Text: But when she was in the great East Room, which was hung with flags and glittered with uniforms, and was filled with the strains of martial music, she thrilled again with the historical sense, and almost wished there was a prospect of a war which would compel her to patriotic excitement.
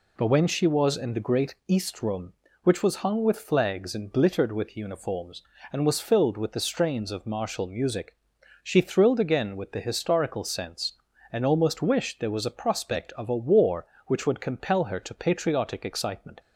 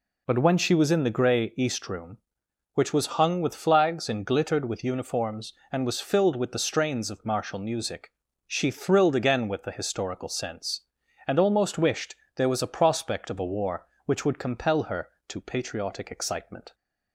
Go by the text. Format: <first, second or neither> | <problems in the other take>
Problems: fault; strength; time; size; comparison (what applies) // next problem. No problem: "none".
first | says "grey" for "great"; at 1.1 s // pauses between "wished" and "there"; slight; at 12.1 s; 0.22 s long